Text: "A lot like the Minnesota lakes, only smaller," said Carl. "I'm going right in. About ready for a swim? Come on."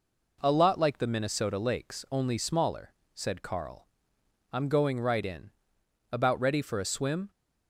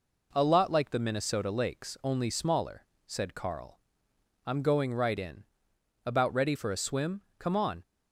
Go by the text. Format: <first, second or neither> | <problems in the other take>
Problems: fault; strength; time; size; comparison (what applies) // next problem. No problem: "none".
second | stops before "Come on"; at 7.2 s